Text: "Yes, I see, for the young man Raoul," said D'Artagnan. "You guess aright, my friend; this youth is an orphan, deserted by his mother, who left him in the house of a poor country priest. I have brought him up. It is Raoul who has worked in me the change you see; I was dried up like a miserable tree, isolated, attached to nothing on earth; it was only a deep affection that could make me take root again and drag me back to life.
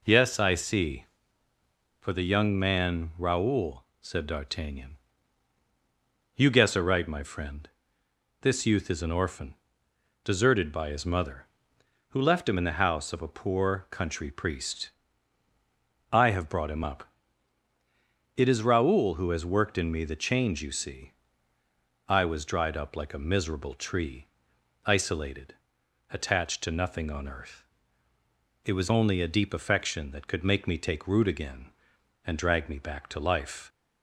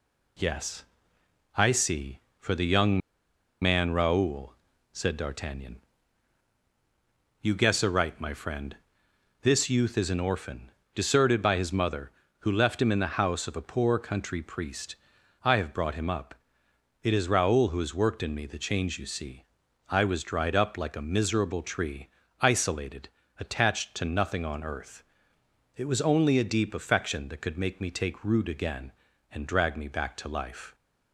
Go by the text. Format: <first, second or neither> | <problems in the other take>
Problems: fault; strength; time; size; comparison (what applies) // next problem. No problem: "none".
first | pauses between "young" and "man"; noticeable; at 3.0 s; 0.62 s long